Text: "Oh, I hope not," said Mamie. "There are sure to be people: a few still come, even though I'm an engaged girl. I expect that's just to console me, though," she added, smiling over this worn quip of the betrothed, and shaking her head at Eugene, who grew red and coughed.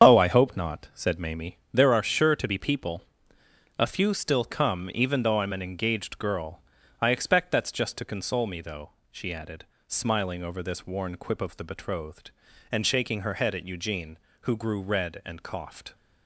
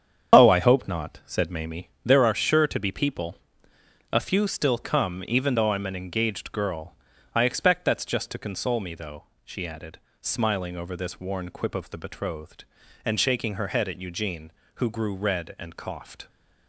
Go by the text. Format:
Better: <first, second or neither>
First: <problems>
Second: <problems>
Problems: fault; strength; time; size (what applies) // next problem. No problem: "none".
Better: neither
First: starts louder than the rest; until 1.1 s; 6.5 dB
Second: starts louder than the rest; until 1.4 s; 6.5 dB